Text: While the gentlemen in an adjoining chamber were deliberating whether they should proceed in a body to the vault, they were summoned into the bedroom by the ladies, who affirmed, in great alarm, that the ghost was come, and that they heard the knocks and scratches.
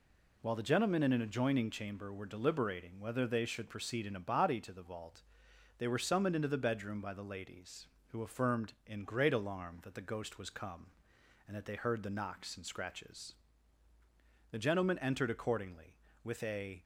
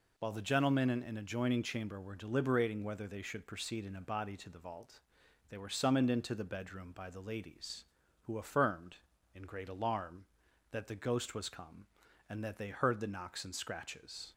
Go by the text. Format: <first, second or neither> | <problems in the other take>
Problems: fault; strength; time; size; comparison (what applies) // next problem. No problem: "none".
second | goes on to say "The gentlemen entered accordingly with a"; strong; from 14.5 s on; 2.3 s long